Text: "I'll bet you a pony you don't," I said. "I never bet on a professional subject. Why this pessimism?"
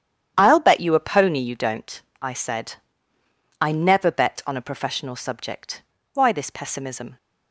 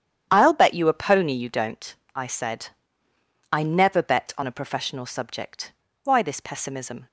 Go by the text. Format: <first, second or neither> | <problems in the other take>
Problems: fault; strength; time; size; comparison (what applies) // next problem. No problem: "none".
neither | starts louder than the rest; strong; the same in both